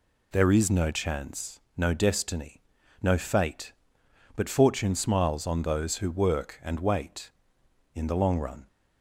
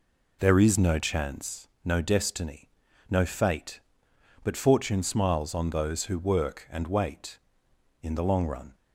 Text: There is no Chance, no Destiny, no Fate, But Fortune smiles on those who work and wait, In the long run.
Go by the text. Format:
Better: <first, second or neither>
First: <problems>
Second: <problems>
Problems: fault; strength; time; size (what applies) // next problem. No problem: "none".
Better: first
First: none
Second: starts louder than the rest; slight; until 1.6 s; 3.5 dB